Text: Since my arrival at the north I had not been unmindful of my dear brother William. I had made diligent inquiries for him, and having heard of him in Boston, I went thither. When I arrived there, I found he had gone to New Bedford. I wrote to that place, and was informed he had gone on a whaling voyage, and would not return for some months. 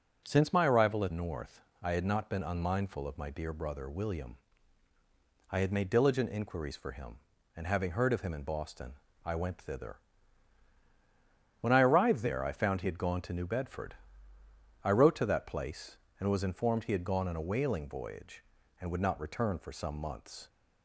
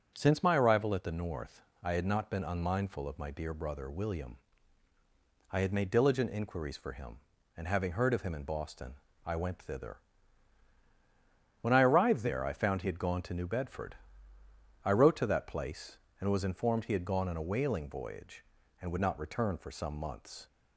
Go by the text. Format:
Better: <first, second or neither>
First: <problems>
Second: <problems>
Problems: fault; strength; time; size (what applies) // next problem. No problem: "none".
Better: second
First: skips "the"; at 1.1 s // pauses between "north" and "I"; slight; at 1.6 s; 0.20 s long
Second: pauses between "north" and "I"; slight; at 1.6 s; 0.20 s long